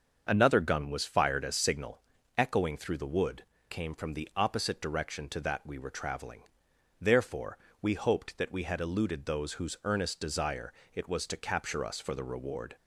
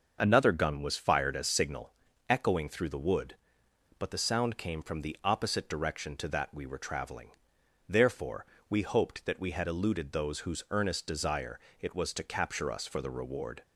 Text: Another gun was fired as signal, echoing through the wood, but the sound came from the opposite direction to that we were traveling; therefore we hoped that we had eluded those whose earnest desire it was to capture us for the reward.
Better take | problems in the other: second | starts louder than the rest; until 1.3 s; 6.5 dB; also in the second // skips "but the sound"; at 3.5 s // pauses between "therefore" and "we"; slight; at 7.5 s; 0.24 s long; slight in the second // pauses between "desire" and "it"; slight; at 10.7 s; 0.20 s long; slight in the second

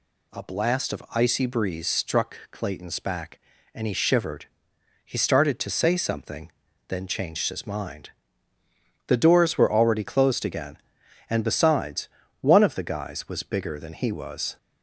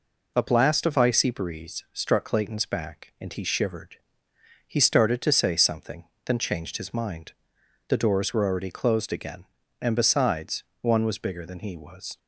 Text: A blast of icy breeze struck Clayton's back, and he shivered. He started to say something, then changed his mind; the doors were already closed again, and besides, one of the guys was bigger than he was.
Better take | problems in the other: first | skips "of the guys"; at 11.0 s

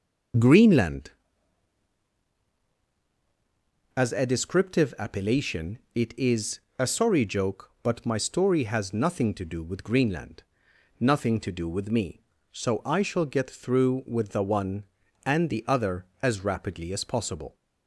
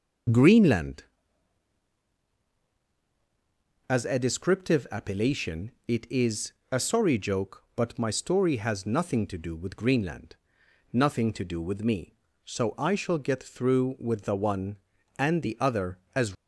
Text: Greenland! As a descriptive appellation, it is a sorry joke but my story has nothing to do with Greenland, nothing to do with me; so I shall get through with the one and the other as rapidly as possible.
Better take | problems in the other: first | pauses between "is" and "a"; slight; at 6.5 s; 0.18 s long; slight in the first // stops before "rapidly as possible"; at 16.3 s

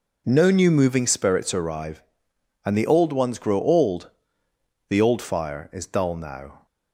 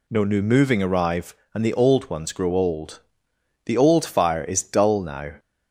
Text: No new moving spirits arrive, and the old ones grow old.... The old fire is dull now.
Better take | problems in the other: first | skips "spirits"; at 0.8 s

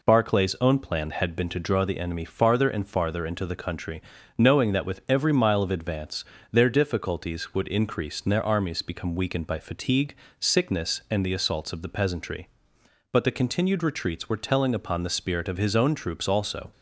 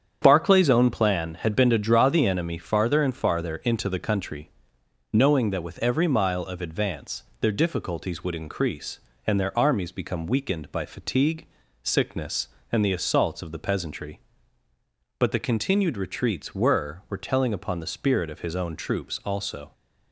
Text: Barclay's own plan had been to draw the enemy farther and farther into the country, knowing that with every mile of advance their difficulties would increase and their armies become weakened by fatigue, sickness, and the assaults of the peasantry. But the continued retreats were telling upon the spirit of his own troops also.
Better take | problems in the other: first | starts louder than the rest; strong; until 1.2 s; 8 dB // pauses between "advance" and "their"; slight; at 7.2 s; 0.18 s long; slight in the first // says "were" twice; at 17.0 s

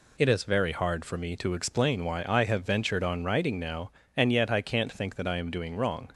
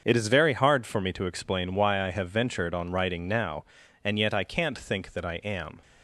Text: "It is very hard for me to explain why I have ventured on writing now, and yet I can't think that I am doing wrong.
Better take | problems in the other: first | starts louder than the rest; until 1.0 s; 6.5 dB // stops before "doing wrong"; at 5.8 s

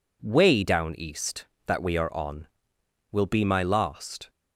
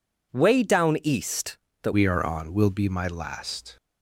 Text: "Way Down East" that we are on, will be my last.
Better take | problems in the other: first | changes voice at "we"; from 1.9 s on; 1.8 s long

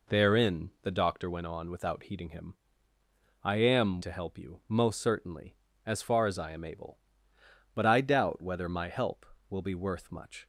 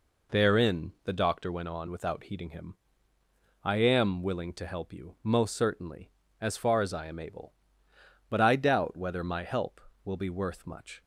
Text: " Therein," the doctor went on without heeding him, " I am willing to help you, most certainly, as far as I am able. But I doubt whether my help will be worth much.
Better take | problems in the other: second | skips "willing"; at 4.0 s

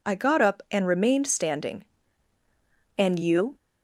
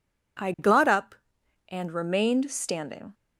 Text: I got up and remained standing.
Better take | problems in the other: second | goes on to say "And you"; from 2.9 s on; 0.57 s long

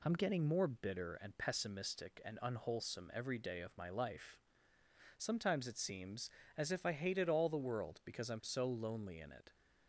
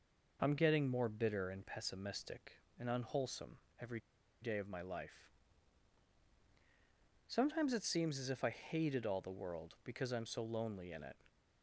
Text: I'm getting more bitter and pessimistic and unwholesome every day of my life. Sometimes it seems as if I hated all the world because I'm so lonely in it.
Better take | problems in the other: first | pauses between "unwholesome" and "every"; slight; at 3.5 s; 0.22 s long // pauses between "every" and "day"; at 3.9 s; 0.43 s long

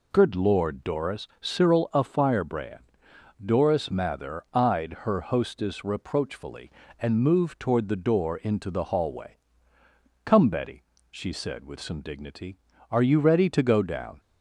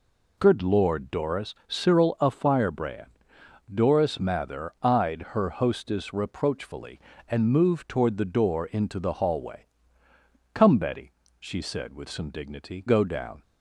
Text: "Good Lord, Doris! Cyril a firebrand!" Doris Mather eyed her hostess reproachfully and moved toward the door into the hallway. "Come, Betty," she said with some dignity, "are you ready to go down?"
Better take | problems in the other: first | skips "are you ready to"; at 12.8 s

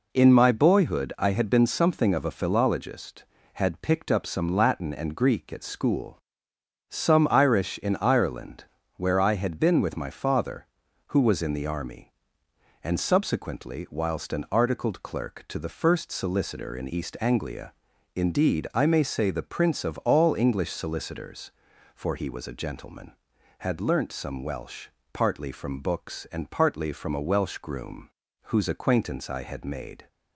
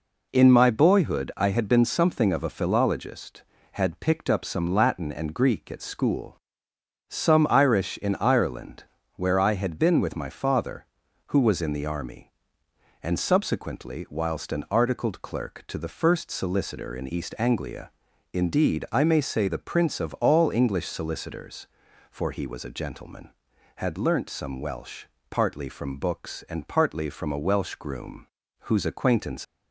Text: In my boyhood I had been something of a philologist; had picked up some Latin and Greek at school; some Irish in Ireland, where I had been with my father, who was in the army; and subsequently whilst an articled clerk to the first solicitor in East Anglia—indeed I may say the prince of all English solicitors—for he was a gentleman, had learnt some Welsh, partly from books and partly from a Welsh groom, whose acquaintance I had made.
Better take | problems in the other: first | stops before "I had made"; at 29.4 s

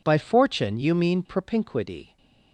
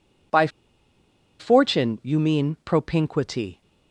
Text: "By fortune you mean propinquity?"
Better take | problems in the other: first | pauses between "By" and "fortune"; noticeable; at 0.4 s; 0.91 s long

